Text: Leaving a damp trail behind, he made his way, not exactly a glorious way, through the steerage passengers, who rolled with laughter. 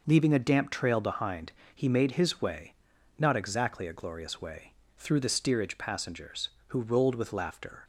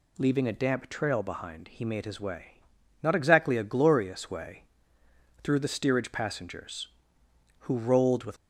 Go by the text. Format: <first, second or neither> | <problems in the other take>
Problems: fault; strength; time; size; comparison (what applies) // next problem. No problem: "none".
first | stops before "laughter"; at 8.3 s